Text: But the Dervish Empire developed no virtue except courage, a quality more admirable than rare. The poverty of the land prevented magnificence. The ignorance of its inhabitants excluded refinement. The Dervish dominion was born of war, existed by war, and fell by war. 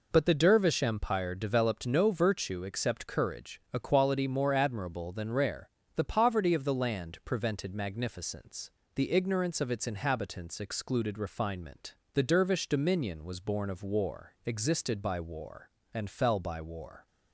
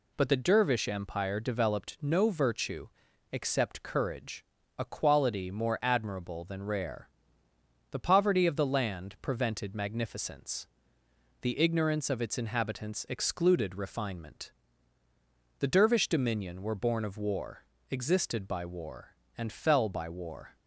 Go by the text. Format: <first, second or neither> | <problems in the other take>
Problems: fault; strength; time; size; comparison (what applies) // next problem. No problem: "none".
first | pauses between "virtue" and "except"; at 2.8 s; 0.42 s long // says "were" for "was"; at 16.6 s